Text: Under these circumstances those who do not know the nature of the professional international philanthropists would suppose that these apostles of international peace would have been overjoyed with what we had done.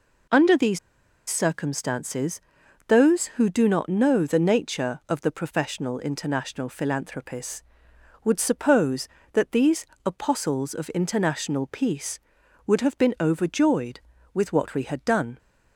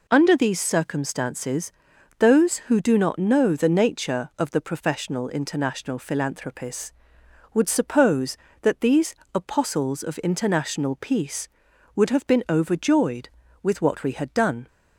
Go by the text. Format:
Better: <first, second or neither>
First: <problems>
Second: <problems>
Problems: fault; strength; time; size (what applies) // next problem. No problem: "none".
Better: second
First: pauses between "these" and "circumstances"; noticeable; at 0.7 s; 0.50 s long // pauses between "circumstances" and "those"; noticeable; at 2.4 s; 0.46 s long // pauses between "these" and "apostles"; slight; at 9.8 s; 0.18 s long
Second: pauses between "circumstances" and "those"; noticeable; at 1.7 s; 0.46 s long // pauses between "these" and "apostles"; slight; at 9.1 s; 0.18 s long